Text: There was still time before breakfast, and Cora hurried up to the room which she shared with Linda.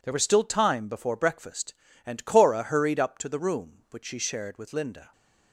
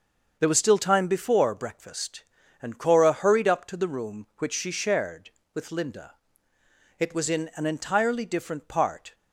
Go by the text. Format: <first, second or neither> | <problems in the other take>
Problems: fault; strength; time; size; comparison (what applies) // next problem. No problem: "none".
first | starts louder than the rest; until 1.4 s; 6 dB // goes on to say "It was in an entirely different part"; strong; from 6.9 s on; 2.1 s long